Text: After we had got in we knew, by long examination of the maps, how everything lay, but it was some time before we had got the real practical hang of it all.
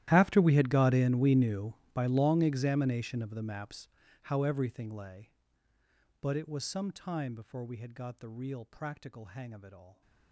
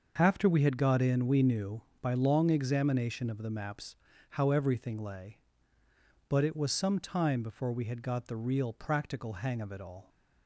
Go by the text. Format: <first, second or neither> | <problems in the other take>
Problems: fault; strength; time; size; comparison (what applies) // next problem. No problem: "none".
second | gets quieter; strong; throughout; 23 dB // starts louder than the rest; strong; until 1.1 s; 13 dB; also in the second